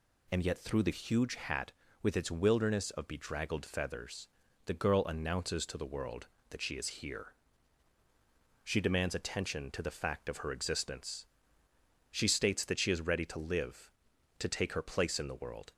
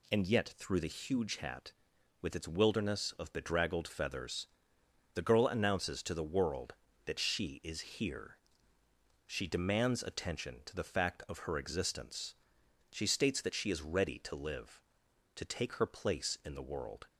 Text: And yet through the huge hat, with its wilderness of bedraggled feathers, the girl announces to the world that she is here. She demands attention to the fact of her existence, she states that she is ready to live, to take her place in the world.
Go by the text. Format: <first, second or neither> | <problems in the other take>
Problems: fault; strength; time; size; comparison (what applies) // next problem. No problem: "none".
neither | none